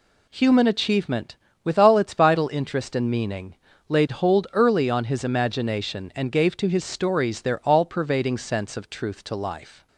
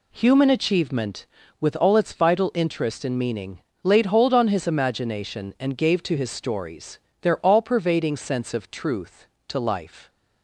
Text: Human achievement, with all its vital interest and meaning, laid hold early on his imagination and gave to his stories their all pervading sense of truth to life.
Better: first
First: none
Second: skips "early"; at 4.3 s // pauses between "stories" and "their"; slight; at 6.9 s; 0.24 s long

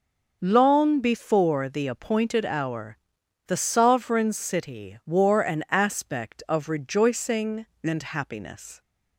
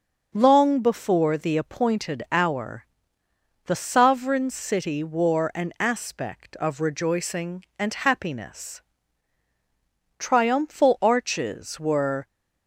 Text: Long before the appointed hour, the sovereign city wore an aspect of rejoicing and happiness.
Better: first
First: none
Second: starts louder than the rest; noticeable; until 1.3 s; 6 dB // goes on to say "Triumphal arches were"; strong; from 10.1 s on; 2.0 s long

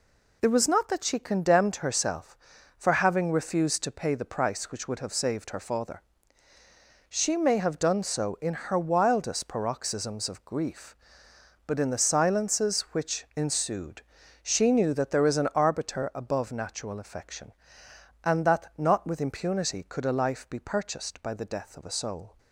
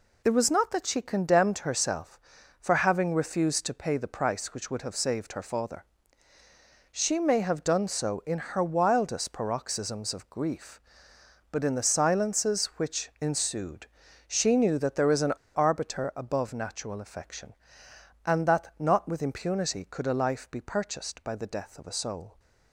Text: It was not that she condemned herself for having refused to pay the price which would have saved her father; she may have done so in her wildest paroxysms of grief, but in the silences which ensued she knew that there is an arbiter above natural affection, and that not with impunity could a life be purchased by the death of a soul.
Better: first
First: pauses between "ensued" and "she"; at 14.0 s; 0.40 s long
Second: pauses between "ensued" and "she"; at 13.8 s; 0.40 s long // pauses between "an" and "arbiter"; slight; at 15.3 s; 0.20 s long

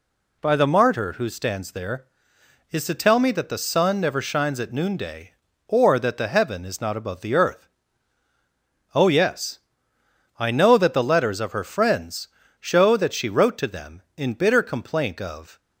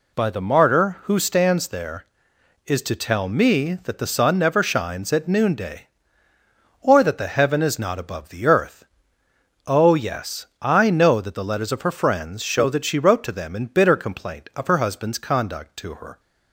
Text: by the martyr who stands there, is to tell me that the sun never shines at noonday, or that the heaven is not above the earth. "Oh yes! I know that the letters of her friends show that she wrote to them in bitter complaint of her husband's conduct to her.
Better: second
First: pauses between "friends" and "show"; slight; at 12.2 s; 0.32 s long // stops before "her husband's conduct to her"; at 15.5 s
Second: none

